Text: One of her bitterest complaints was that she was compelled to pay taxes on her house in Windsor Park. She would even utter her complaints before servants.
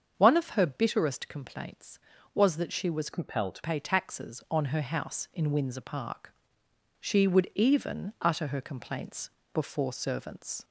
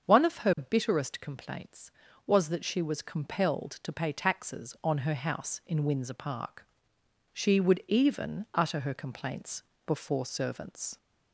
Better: second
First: starts louder than the rest; until 1.1 s; 7 dB // changes voice from "compelled" to "to"; from 3.1 to 3.6 s; 0.5 s long // pauses between "complaints" and "before"; slight; at 9.3 s; 0.22 s long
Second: starts louder than the rest; until 1.1 s; 7 dB // pauses between "complaints" and "before"; slight; at 9.6 s; 0.22 s long

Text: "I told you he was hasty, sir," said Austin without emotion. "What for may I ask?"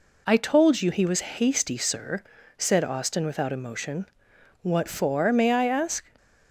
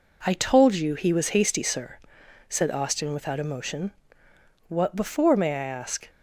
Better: first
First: none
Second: says "before" for "for"; at 4.9 s

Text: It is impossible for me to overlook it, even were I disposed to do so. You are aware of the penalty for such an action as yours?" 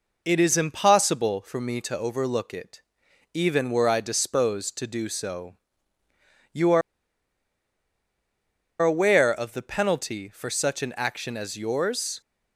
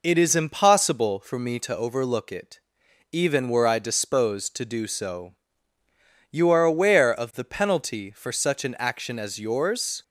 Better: second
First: pauses between "are" and "aware"; strong; at 6.8 s; 2.0 s long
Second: none

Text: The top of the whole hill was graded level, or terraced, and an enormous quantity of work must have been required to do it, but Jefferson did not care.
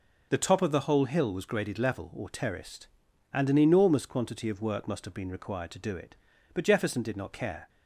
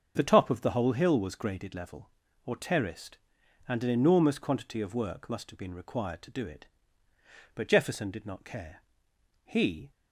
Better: first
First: none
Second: starts louder than the rest; until 1.1 s; 7 dB // goes on to say "He"; slight; from 9.4 s on; 0.46 s long

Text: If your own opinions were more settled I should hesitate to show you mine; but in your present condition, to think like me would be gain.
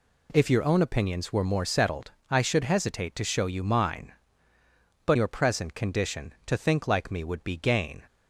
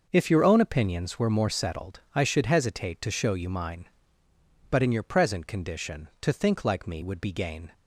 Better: second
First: pauses between "settled" and "I"; slight; at 2.1 s; 0.18 s long // skips "in"; at 5.1 s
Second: pauses between "settled" and "I"; slight; at 1.9 s; 0.16 s long

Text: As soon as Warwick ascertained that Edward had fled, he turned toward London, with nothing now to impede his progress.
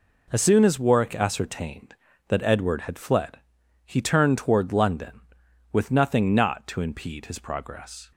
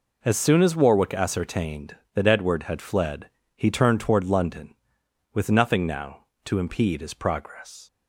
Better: second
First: says "not" for "now"; at 6.3 s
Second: none

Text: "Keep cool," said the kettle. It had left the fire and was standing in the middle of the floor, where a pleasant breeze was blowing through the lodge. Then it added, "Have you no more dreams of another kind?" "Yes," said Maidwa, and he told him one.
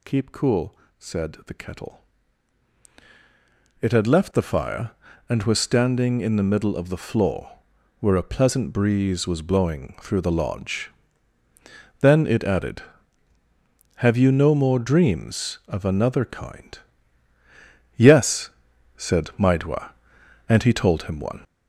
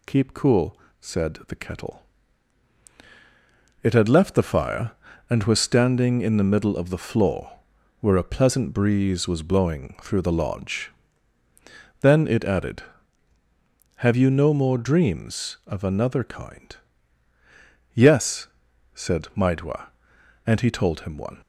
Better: second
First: gets louder; noticeable; throughout; 6 dB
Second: none

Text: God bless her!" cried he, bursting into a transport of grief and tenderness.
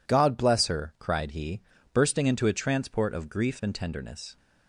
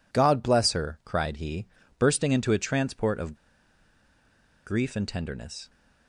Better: first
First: none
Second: pauses between "of" and "grief"; strong; at 3.3 s; 1.3 s long

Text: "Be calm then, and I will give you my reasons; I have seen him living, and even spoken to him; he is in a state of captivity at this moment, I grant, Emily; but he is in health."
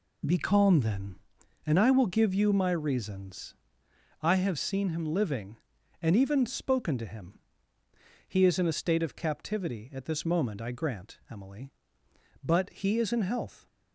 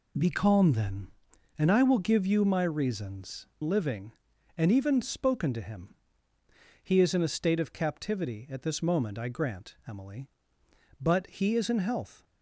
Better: first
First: none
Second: skips "I have seen him"; at 3.5 s

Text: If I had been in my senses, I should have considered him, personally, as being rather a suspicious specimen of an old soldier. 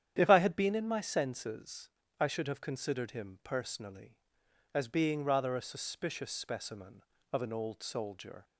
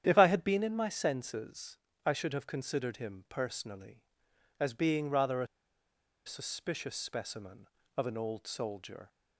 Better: first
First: starts louder than the rest; strong; until 1.1 s; 9.5 dB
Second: starts louder than the rest; strong; until 1.0 s; 9.5 dB // pauses between "a" and "suspicious"; noticeable; at 5.4 s; 0.79 s long

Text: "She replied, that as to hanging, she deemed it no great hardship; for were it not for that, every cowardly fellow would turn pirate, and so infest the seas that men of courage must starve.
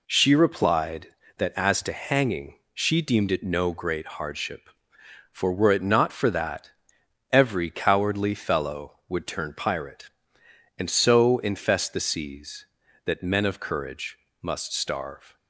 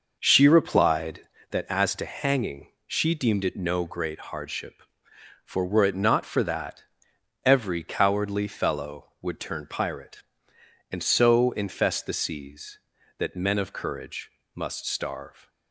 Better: first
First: pauses between "courage" and "must"; slight; at 14.1 s; 0.24 s long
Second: starts louder than the rest; noticeable; until 1.5 s; 5.5 dB // pauses between "courage" and "must"; slight; at 14.3 s; 0.24 s long

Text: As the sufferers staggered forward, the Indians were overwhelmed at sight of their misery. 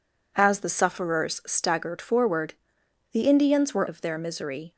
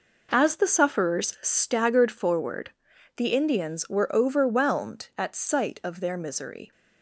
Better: second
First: skips "overwhelmed at sight"; at 3.8 s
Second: none

